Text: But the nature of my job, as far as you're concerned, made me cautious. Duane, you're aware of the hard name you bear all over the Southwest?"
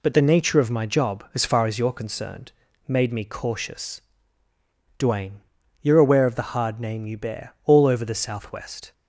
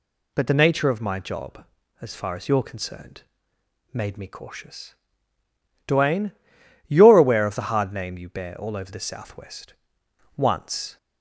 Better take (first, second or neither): first